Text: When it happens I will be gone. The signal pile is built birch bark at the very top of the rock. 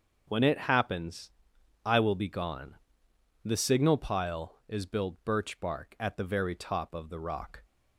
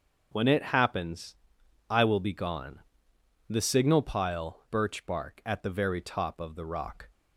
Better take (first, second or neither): first